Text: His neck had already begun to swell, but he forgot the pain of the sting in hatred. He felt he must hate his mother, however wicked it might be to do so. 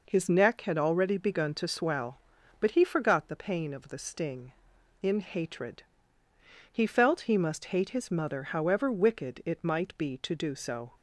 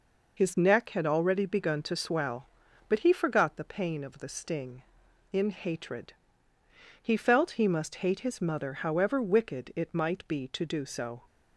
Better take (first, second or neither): first